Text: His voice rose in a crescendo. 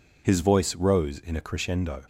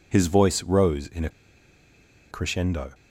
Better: first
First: none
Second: pauses between "a" and "crescendo"; at 1.2 s; 1.0 s long

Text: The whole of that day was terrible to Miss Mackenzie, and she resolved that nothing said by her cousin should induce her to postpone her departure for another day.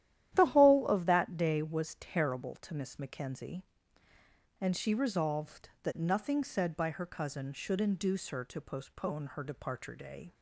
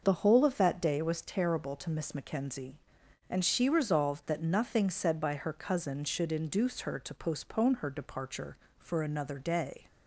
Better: second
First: starts louder than the rest; strong; until 1.3 s; 12 dB // skips "for another"; at 9.9 s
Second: starts louder than the rest; noticeable; until 1.0 s; 6 dB

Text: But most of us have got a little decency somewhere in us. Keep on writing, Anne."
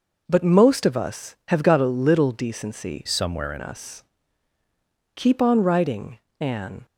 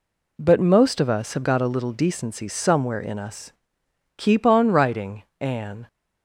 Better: second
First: changes voice from "somewhere" to "in"; from 3.0 to 3.6 s; 0.6 s long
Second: none

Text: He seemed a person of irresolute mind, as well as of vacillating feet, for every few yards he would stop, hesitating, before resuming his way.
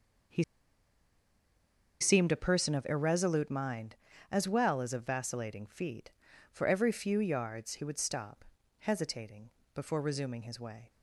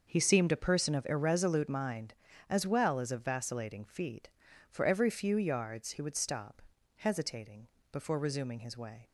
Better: second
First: starts louder than the rest; noticeable; until 2.9 s; 6 dB // pauses between "He" and "seemed"; strong; at 0.4 s; 1.5 s long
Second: starts louder than the rest; noticeable; until 1.1 s; 6 dB

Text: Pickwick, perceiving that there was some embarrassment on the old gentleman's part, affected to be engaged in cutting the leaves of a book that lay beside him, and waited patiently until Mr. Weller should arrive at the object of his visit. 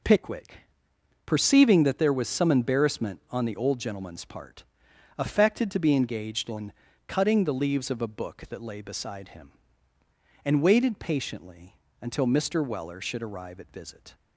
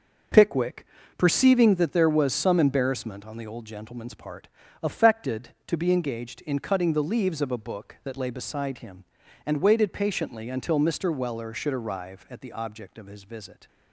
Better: second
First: pauses between "in" and "cutting"; slight; at 6.7 s; 0.34 s long // pauses between "patiently" and "until"; slight; at 11.7 s; 0.24 s long // skips "the object of his"; at 13.7 s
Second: none

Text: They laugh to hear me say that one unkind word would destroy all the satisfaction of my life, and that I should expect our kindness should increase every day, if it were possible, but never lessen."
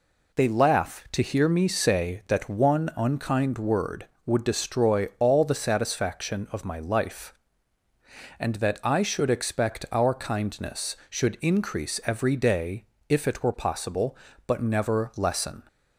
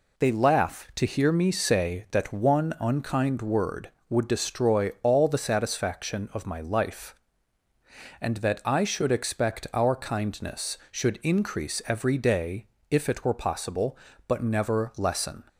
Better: neither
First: none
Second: none

